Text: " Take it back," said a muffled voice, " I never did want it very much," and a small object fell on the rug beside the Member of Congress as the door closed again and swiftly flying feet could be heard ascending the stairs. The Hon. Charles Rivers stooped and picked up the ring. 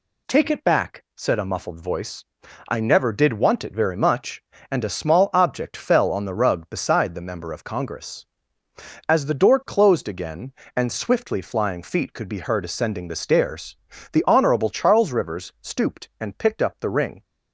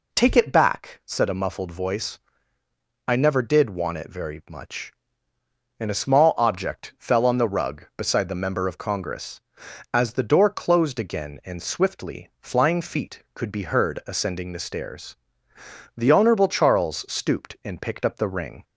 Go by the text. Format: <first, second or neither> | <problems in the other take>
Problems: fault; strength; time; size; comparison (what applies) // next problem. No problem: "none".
first | skips "Rivers"; at 17.0 s